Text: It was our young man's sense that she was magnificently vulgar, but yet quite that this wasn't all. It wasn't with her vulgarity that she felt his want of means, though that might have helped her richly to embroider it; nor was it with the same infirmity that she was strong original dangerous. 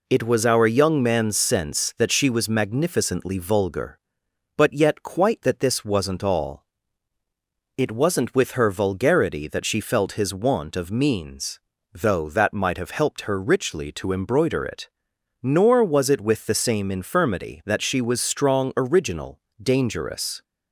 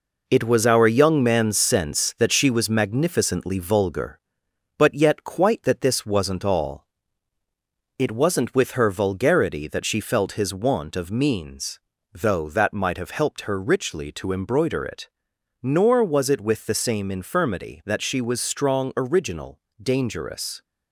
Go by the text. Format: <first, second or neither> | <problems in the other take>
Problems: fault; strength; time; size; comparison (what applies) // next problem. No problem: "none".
first | gets quieter; noticeable; throughout; 5.5 dB // pauses between "original" and "dangerous"; slight; at 19.6 s; 0.18 s long; slight in the first